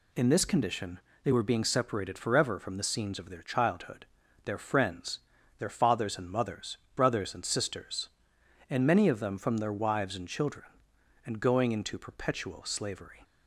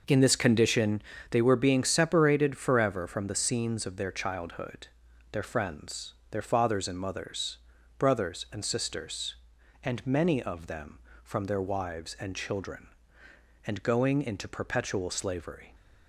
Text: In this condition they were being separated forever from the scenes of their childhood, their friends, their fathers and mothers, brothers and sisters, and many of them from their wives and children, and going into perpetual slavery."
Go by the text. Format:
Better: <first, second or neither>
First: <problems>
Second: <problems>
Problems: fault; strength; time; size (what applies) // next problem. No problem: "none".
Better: first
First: pauses between "condition" and "they"; slight; at 0.9 s; 0.24 s long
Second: starts louder than the rest; noticeable; until 1.5 s; 5.5 dB // pauses between "condition" and "they"; slight; at 1.0 s; 0.28 s long